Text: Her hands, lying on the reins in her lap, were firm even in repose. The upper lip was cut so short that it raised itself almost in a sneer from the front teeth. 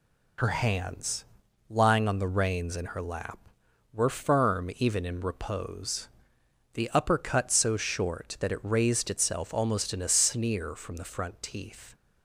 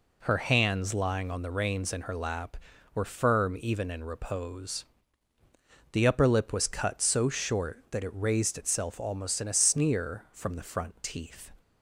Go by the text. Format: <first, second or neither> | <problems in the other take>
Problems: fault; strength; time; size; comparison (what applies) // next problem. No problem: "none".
second | skips "lip was"; at 7.1 s